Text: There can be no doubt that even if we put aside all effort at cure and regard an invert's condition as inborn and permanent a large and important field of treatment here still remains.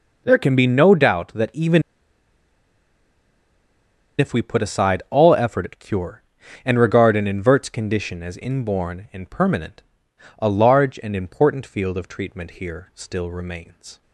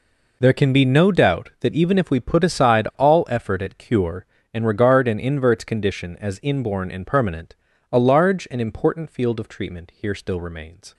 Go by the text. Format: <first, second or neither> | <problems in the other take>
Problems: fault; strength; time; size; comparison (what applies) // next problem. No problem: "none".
second | pauses between "even" and "if"; strong; at 1.8 s; 2.3 s long // pauses between "permanent" and "a"; noticeable; at 9.8 s; 0.56 s long; slight in the second